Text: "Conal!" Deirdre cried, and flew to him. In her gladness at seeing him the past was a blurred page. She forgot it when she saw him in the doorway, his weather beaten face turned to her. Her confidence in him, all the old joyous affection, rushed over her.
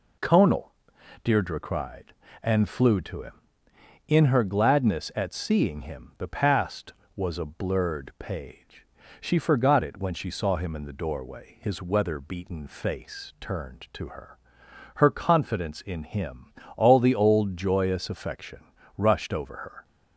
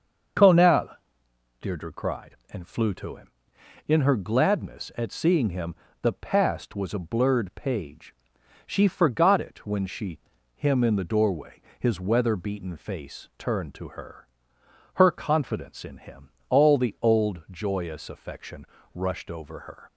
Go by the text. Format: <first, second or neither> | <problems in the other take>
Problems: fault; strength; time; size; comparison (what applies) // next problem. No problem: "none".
first | starts louder than the rest; until 2.1 s; 6.5 dB // pauses between "him" and "the"; slight; at 5.7 s; 0.28 s long // skips "saw"; at 10.3 s